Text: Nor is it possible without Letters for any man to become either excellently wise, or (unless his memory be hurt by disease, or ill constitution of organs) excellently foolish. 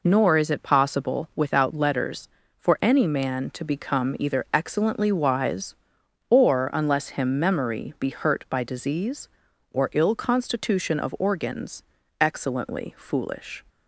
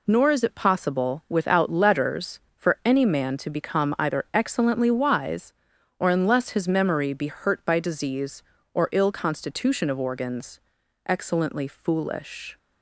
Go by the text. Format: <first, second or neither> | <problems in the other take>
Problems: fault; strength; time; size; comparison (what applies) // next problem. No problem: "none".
second | says "him" for "his"; at 7.0 s